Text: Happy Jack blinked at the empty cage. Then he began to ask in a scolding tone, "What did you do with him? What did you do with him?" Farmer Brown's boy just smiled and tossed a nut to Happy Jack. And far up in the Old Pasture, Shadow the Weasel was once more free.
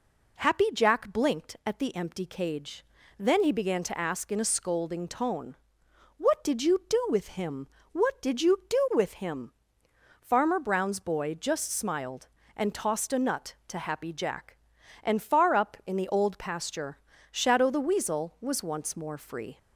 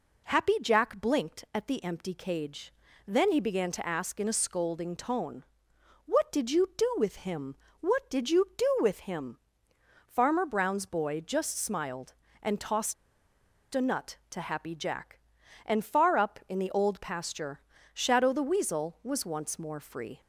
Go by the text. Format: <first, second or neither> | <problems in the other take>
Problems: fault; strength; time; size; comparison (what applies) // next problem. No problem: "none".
first | pauses between "tossed" and "a"; noticeable; at 12.9 s; 0.79 s long